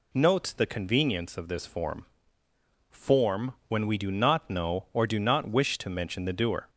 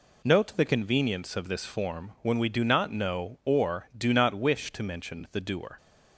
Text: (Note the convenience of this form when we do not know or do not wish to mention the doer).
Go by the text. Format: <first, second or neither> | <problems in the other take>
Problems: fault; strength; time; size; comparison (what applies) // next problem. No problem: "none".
second | says "form" twice; at 2.8 s